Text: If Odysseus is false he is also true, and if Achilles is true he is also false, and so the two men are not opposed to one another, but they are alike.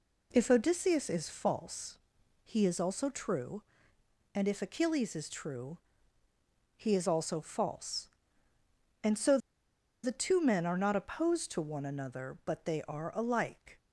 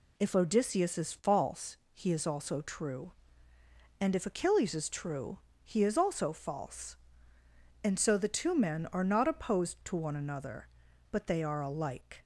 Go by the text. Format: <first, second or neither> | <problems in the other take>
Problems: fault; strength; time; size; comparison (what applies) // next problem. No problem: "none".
second | pauses between "false" and "he"; noticeable; at 1.9 s; 0.46 s long; slight in the second // pauses between "true" and "he"; noticeable; at 5.7 s; 0.98 s long; slight in the second // pauses between "so" and "the"; noticeable; at 9.3 s; 0.66 s long